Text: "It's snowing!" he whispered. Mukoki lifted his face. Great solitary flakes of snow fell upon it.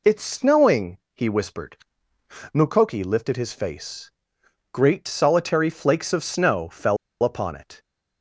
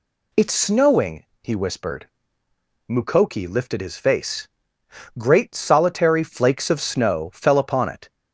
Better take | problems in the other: second | pauses between "fell" and "upon"; slight; at 6.9 s; 0.26 s long

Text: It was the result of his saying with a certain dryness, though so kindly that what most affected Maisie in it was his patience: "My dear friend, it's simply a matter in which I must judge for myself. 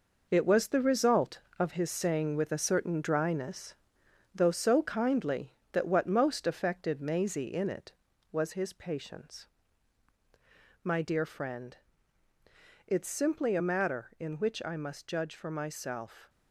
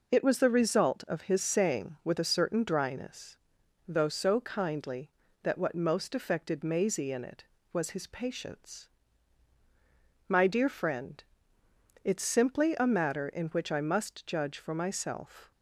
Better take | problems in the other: second | gets quieter; strong; throughout; 8 dB

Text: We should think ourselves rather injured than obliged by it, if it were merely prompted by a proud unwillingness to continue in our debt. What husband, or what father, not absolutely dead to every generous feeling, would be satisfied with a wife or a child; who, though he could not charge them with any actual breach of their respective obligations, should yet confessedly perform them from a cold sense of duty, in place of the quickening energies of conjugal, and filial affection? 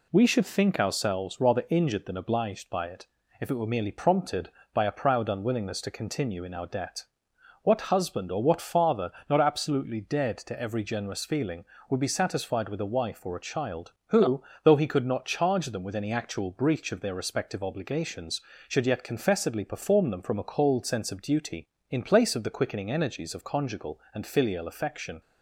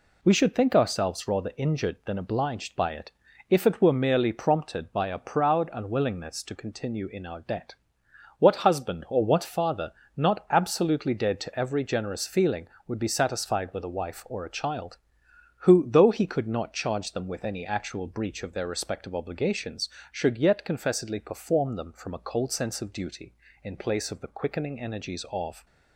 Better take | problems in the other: first | stops before "conjugal and filial affection"; at 25.6 s

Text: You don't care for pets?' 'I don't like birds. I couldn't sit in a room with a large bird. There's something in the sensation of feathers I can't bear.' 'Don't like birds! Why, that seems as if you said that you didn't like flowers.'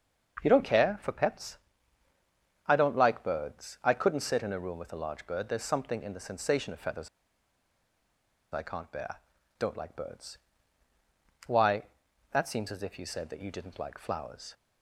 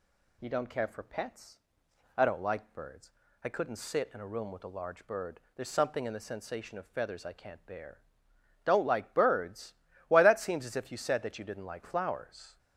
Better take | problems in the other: second | starts louder than the rest; until 1.4 s; 6.5 dB // pauses between "feathers" and "I"; strong; at 7.0 s; 1.4 s long

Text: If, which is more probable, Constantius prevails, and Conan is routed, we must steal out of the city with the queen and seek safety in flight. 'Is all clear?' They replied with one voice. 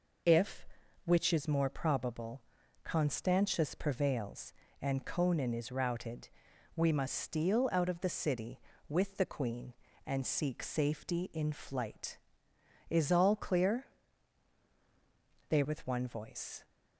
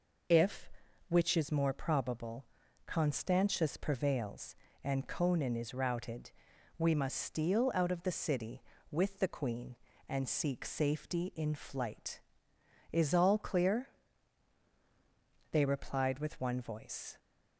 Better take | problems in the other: second | skips "replied"; at 15.6 s

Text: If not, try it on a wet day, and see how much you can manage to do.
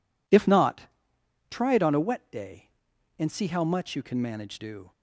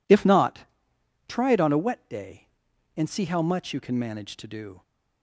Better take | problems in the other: second | skips "to"; at 4.5 s

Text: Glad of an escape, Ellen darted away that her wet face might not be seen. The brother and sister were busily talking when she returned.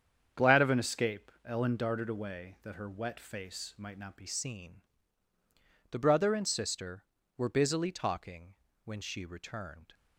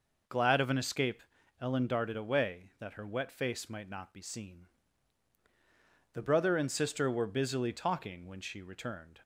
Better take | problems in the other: second | starts louder than the rest; strong; until 1.4 s; 8 dB // changes voice at "seen"; from 4.2 s on; 5.7 s long // pauses between "talking" and "when"; slight; at 8.5 s; 0.30 s long

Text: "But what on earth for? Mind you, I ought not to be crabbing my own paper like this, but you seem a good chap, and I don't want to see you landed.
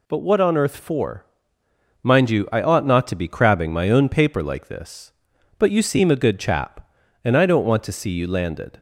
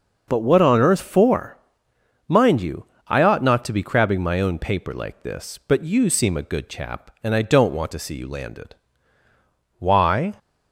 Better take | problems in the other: first | goes on to say "Why"; from 9.7 s on; 0.56 s long

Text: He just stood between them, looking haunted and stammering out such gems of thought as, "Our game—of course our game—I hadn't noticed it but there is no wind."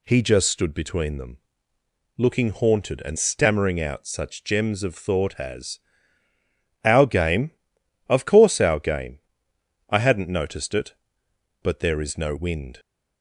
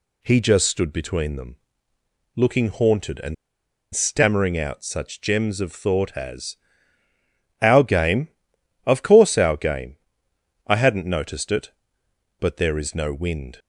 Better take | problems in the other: first | pauses between "and" and "stammering"; noticeable; at 3.3 s; 0.59 s long

